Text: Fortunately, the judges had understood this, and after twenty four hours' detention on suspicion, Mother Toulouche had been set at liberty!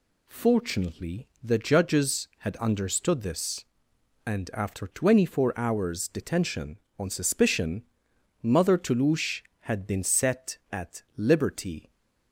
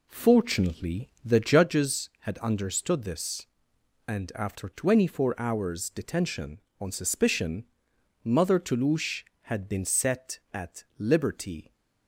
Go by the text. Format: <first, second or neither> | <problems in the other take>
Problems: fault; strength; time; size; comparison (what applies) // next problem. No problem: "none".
first | starts louder than the rest; slight; until 1.7 s; 3 dB